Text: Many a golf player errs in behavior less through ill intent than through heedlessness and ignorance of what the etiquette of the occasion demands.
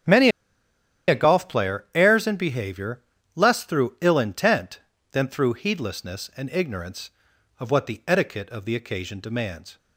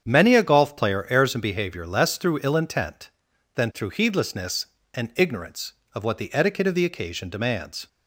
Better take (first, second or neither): second